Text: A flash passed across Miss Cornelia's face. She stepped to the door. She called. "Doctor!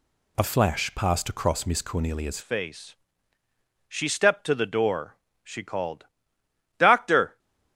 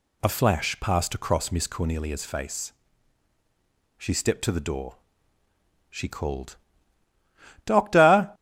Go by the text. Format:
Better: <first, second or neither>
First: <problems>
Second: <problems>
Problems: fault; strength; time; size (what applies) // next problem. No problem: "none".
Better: second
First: changes voice at "face"; from 2.4 s on; 4.9 s long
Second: none